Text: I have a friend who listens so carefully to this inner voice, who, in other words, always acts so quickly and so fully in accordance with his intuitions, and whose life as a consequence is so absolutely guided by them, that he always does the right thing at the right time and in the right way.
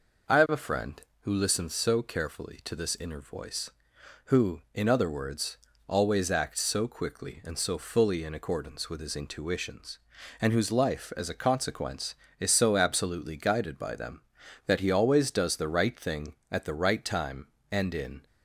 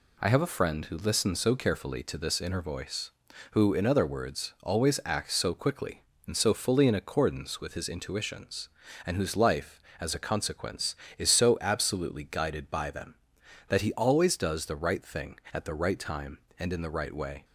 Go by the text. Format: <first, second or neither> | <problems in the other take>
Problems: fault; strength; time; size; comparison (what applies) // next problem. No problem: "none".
second | stops before "the right way"; at 18.2 s